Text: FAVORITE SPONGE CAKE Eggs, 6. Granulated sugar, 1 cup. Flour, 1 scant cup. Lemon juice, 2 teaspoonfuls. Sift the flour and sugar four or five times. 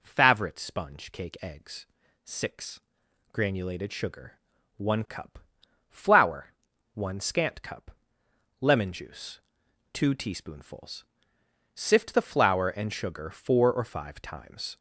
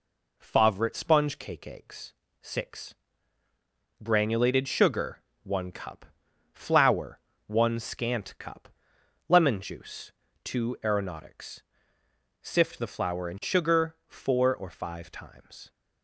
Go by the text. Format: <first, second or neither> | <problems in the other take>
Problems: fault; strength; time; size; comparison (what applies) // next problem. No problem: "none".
first | says "aeronautics" for "teaspoonfuls"; at 10.8 s